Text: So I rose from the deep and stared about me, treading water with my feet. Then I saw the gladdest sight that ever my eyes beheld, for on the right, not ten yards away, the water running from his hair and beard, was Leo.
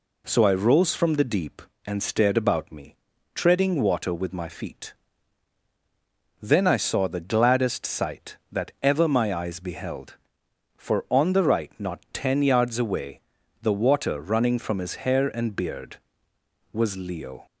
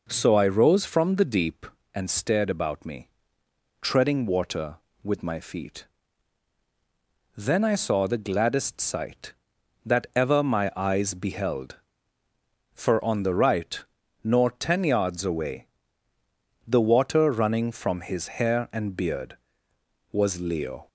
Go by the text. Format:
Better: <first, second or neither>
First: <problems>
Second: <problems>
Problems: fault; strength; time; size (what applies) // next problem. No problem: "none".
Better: first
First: none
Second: says "nor" for "not"; at 14.2 s